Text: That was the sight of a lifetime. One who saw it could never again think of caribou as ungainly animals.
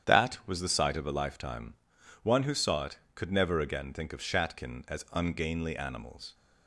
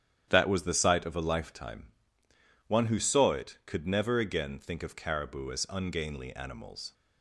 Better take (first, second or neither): second